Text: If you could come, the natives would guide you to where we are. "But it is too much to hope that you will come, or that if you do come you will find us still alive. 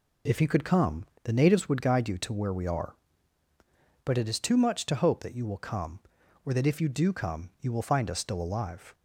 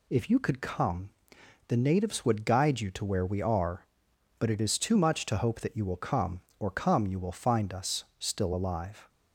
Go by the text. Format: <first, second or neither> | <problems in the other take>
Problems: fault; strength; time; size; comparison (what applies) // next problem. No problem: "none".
first | skips "that if you do"; at 6.7 s